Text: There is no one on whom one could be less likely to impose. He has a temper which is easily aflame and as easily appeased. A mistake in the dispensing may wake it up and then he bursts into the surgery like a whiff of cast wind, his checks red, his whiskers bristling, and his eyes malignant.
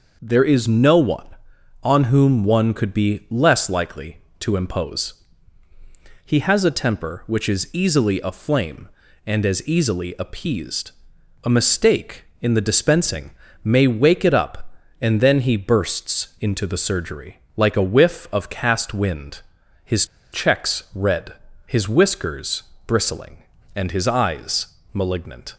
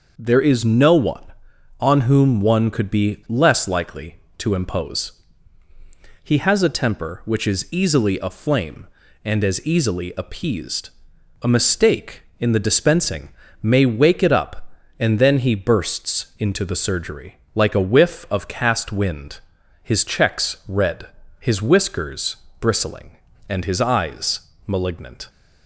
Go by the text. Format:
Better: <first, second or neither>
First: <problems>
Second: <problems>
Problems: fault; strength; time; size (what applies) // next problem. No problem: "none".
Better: second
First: pauses between "dispensing" and "may"; slight; at 13.3 s; 0.32 s long // pauses between "surgery" and "like"; slight; at 17.3 s; 0.18 s long // pauses between "his" and "checks"; slight; at 20.0 s; 0.27 s long // pauses between "whiskers" and "bristling"; slight; at 22.6 s; 0.22 s long // pauses between "eyes" and "malignant"; slight; at 24.6 s; 0.26 s long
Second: pauses between "dispensing" and "may"; slight; at 13.2 s; 0.32 s long // pauses between "surgery" and "like"; slight; at 17.3 s; 0.18 s long // pauses between "whiskers" and "bristling"; slight; at 22.3 s; 0.22 s long // pauses between "eyes" and "malignant"; slight; at 24.4 s; 0.26 s long